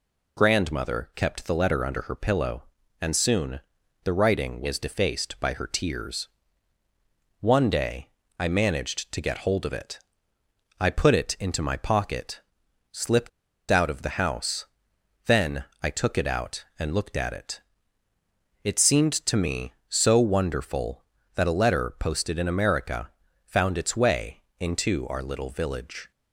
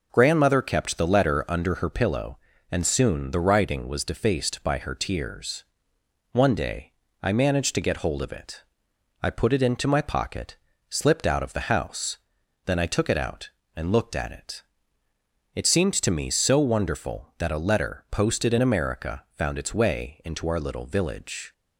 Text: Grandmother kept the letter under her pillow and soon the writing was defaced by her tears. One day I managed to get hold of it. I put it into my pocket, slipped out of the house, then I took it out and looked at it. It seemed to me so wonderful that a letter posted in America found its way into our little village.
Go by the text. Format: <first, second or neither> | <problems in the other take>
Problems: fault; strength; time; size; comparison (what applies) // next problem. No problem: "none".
second | pauses between "soon" and "the"; noticeable; at 3.5 s; 0.46 s long // pauses between "day" and "I"; slight; at 8.0 s; 0.28 s long; slight in the second // pauses between "slipped" and "out"; at 13.2 s; 0.40 s long // pauses between "then" and "I"; slight; at 15.6 s; 0.18 s long // pauses between "America" and "found"; at 23.0 s; 0.38 s long // pauses between "way" and "into"; slight; at 24.4 s; 0.16 s long